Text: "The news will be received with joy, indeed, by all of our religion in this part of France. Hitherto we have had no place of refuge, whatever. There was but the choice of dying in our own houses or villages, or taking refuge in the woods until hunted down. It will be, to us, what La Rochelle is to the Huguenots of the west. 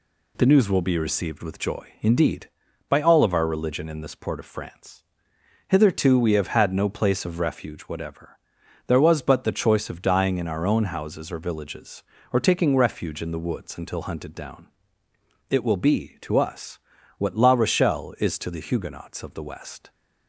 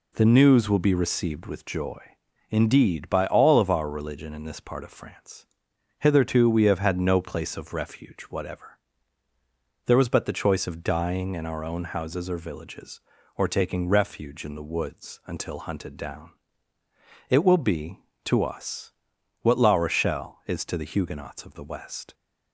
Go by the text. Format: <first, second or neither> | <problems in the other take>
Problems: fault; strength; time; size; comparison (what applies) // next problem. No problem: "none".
second | says "port" for "part"; at 4.1 s